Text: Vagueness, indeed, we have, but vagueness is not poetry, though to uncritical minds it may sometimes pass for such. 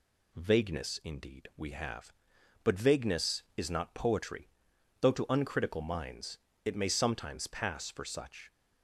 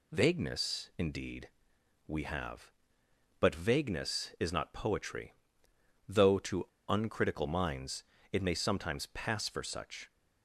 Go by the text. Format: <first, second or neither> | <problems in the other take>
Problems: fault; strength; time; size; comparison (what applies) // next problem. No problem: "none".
first | pauses between "to" and "uncritical"; slight; at 6.6 s; 0.24 s long // pauses between "minds" and "it"; slight; at 8.0 s; 0.30 s long; slight in the first